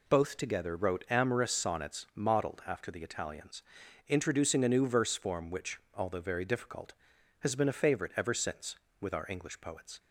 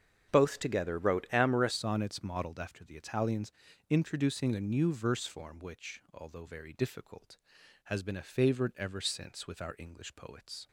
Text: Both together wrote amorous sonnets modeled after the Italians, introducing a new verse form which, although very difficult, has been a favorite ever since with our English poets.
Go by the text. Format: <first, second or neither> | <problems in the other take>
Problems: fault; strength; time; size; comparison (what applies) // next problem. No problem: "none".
first | starts louder than the rest; strong; until 1.3 s; 7.5 dB // changes voice at "sonnets"; from 1.7 s on; 8.9 s long